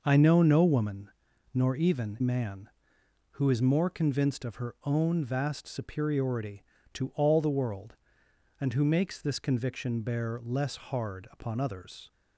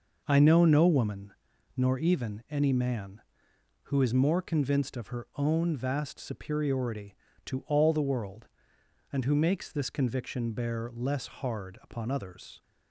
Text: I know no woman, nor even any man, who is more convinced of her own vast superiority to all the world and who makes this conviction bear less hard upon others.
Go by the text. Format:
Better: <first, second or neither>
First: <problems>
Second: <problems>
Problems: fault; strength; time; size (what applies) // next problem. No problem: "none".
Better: second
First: skips "any"; at 2.2 s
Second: none